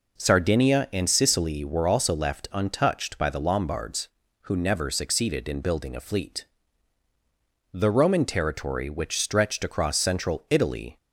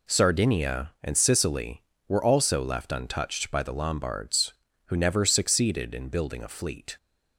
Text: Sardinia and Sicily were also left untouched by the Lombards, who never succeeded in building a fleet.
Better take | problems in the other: second | goes on to say "The Roman territory which stretched across Central Italy"; strong; from 7.7 s on; 3.2 s long

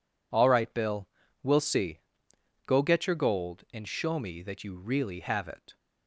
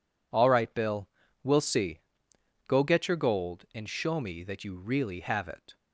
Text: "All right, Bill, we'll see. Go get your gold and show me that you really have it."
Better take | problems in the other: neither | none

